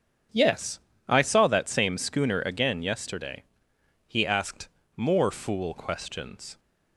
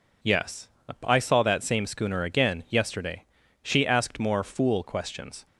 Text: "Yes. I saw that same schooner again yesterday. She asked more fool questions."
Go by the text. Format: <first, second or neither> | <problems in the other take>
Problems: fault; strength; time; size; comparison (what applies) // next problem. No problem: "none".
second | starts louder than the rest; strong; until 1.5 s; 7 dB // says "He" for "She"; at 4.0 s // pauses between "asked" and "more"; slight; at 4.6 s; 0.28 s long